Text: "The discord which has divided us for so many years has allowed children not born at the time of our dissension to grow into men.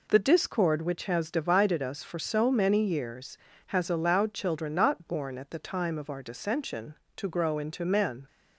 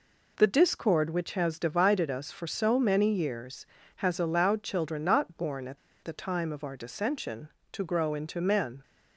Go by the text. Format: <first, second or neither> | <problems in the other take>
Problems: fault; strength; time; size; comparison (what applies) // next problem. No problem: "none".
first | pauses between "at" and "the"; slight; at 5.7 s; 0.26 s long